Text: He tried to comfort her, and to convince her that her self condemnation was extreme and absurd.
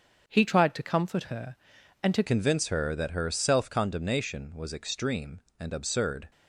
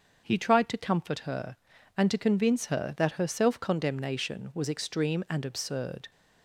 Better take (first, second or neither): second